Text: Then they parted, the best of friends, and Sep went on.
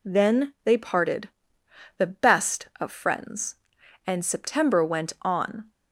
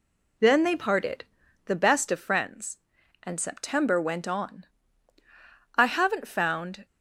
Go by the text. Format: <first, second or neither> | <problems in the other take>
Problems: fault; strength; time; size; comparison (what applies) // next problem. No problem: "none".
first | goes on to say "I haven't found"; noticeable; from 5.7 s on; 1.1 s long